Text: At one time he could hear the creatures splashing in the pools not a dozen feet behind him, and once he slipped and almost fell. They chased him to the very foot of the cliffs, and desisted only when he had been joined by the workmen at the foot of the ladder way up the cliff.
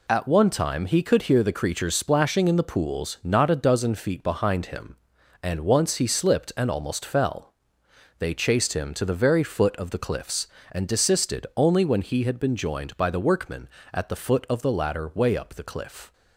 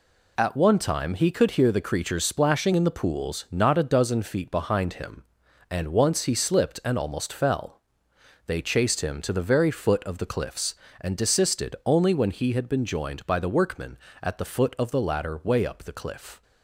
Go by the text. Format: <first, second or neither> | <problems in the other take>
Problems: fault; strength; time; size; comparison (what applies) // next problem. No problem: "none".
neither | none